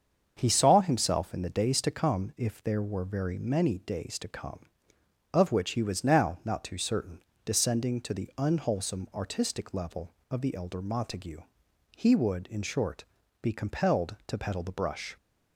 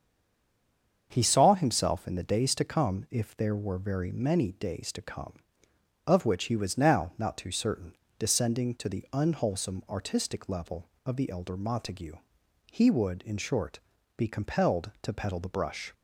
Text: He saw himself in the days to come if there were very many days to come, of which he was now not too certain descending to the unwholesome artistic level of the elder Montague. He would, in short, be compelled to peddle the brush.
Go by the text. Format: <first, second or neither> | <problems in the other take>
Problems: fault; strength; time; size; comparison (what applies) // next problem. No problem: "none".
first | stays silent before the first word; until 1.1 s; 1.1 s long // starts louder than the rest; until 2.1 s; 7 dB; also in the first // pauses between "certain" and "descending"; slight; at 7.9 s; 0.22 s long; slight in the first